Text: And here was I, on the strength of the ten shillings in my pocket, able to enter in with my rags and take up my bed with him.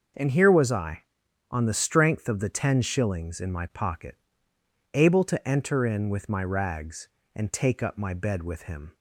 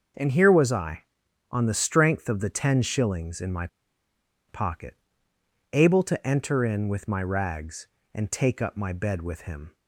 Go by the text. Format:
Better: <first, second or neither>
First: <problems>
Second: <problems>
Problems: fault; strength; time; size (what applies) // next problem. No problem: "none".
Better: first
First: starts louder than the rest; until 1.6 s; 6 dB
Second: starts louder than the rest; until 1.6 s; 6 dB // pauses between "my" and "pocket"; noticeable; at 3.6 s; 0.81 s long